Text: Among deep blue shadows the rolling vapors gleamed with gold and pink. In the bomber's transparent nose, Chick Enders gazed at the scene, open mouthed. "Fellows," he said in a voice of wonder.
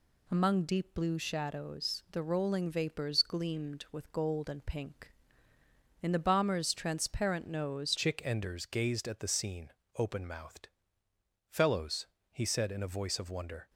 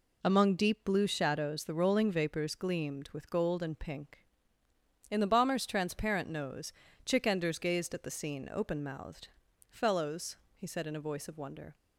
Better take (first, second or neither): second